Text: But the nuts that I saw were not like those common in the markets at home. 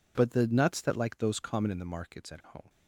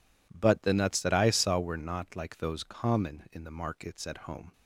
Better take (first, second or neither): second